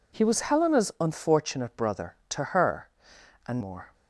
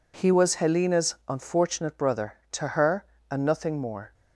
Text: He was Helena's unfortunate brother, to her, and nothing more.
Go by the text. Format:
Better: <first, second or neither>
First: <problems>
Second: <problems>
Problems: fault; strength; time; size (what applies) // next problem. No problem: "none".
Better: second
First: skips "nothing"; at 3.6 s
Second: none